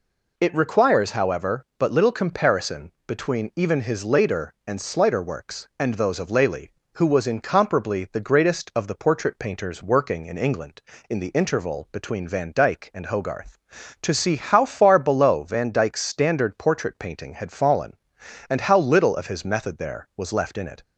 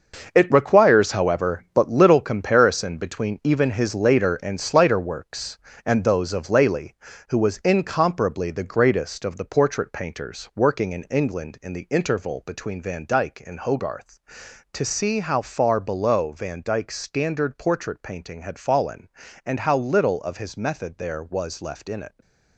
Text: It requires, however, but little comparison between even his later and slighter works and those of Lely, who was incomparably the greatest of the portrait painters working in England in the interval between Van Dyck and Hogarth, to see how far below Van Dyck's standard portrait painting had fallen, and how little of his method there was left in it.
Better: first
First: none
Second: gets quieter; strong; throughout; 10 dB

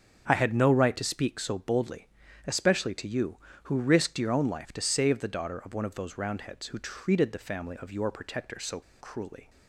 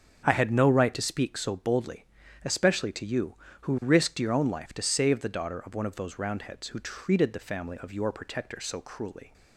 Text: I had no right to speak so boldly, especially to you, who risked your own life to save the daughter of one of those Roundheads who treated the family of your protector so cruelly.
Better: second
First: starts louder than the rest; strong; until 1.2 s; 7.5 dB // pauses between "so" and "cruelly"; slight; at 8.8 s; 0.20 s long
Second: starts louder than the rest; strong; until 1.2 s; 7.5 dB

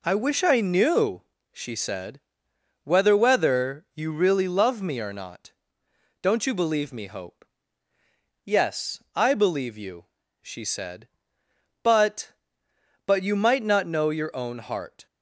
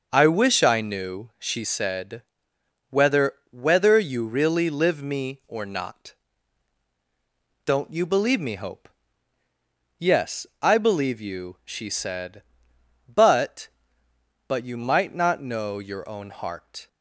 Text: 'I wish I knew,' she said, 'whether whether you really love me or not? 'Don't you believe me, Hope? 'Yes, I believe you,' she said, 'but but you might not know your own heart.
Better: first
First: none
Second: starts louder than the rest; noticeable; until 1.1 s; 6 dB // pauses between "whether" and "whether"; slight; at 3.3 s; 0.18 s long // says "live" for "love"; at 4.6 s

